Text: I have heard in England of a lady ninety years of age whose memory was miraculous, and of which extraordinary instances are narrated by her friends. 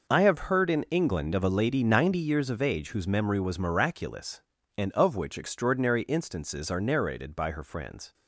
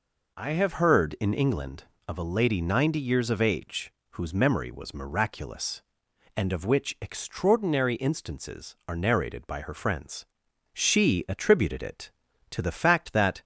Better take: first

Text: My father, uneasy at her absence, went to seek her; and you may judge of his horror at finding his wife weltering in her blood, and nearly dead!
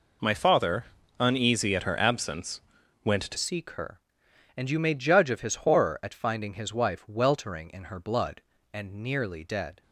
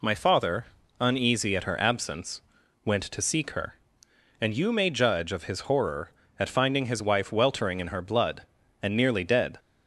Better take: second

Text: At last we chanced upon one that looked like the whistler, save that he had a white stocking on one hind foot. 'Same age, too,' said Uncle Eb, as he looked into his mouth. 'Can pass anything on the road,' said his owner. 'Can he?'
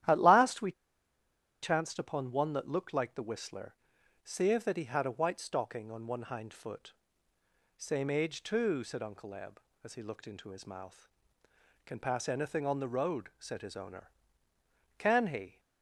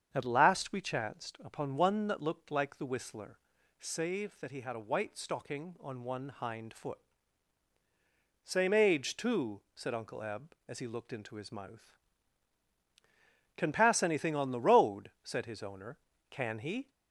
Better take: second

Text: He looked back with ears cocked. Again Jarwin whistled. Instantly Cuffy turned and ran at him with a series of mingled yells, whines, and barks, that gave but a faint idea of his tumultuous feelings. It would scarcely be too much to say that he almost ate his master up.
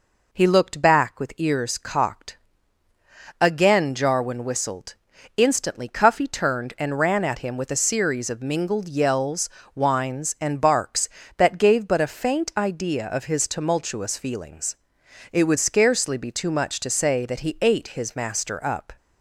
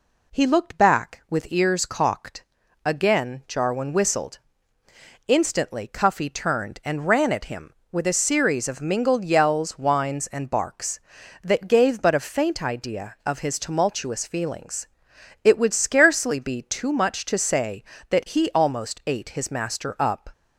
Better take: second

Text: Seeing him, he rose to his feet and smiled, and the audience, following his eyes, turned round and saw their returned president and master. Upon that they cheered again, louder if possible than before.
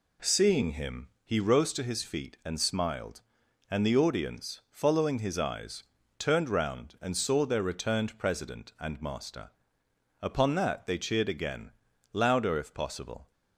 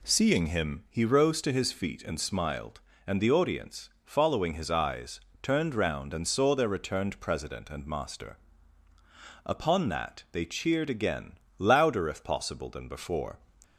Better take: second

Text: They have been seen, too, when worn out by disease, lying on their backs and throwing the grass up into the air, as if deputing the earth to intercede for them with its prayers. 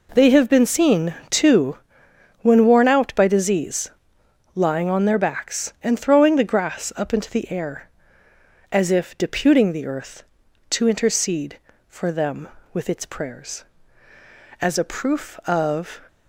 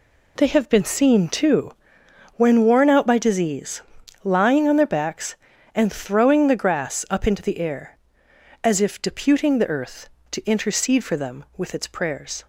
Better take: second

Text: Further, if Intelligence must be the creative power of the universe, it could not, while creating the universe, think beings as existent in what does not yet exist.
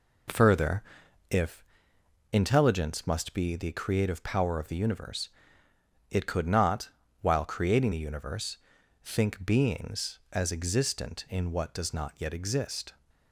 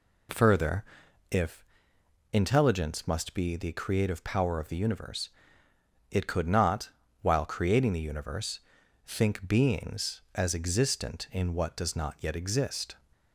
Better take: second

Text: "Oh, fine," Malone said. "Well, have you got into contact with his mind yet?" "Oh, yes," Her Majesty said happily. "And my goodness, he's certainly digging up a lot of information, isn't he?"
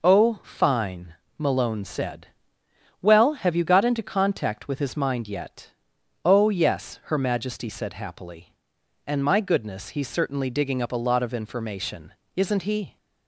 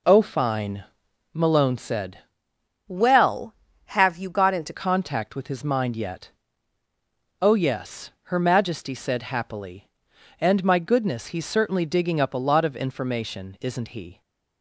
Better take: first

